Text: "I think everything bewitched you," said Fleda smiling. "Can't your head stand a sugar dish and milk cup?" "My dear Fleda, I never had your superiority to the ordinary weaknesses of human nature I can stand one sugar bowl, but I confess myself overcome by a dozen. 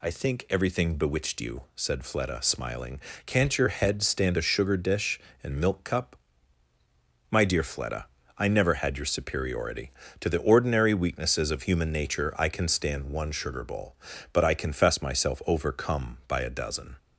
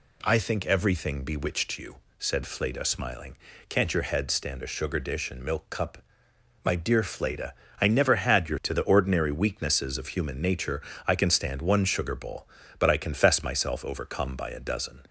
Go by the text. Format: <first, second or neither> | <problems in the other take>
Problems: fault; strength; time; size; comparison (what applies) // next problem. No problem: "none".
first | skips "superiority"; at 8.6 s // pauses between "nature" and "I"; slight; at 10.7 s; 0.28 s long